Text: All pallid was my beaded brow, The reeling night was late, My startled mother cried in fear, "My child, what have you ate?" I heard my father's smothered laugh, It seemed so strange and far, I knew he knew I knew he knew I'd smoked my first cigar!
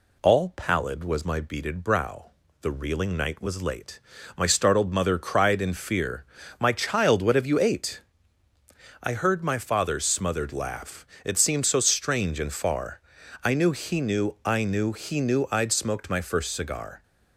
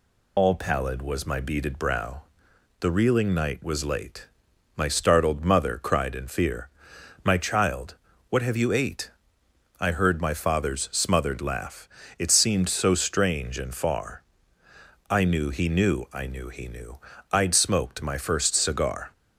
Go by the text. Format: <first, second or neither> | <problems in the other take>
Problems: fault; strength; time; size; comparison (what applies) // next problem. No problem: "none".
first | loses the start of "All"; at 0.3 s; 55 ms // pauses between "knew" and "I'd"; slight; at 16.9 s; 0.32 s long